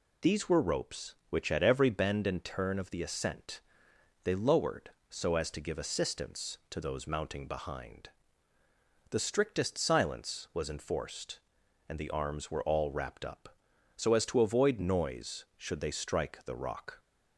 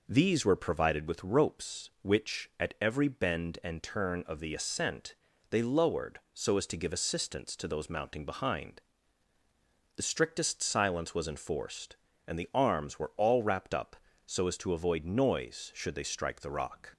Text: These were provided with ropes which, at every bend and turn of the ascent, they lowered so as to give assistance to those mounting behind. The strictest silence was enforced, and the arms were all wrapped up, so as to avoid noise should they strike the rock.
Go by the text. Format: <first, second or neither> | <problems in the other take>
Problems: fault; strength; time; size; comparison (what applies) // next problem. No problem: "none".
second | skips "provided with"; at 0.6 s